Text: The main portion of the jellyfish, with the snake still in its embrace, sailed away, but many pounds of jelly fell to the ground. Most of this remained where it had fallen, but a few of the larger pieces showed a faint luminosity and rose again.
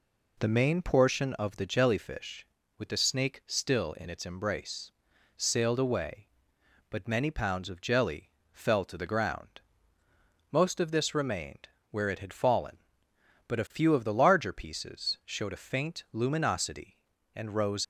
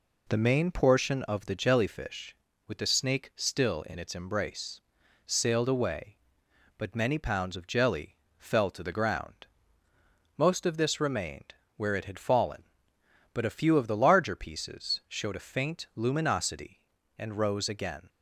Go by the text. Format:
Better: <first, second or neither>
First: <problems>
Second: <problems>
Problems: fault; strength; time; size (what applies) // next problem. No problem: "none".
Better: second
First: pauses between "jelly" and "fell"; slight; at 8.3 s; 0.22 s long // pauses between "remained" and "where"; slight; at 11.6 s; 0.24 s long // stops before "again"; at 17.8 s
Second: pauses between "jelly" and "fell"; slight; at 8.1 s; 0.22 s long // pauses between "remained" and "where"; slight; at 11.5 s; 0.24 s long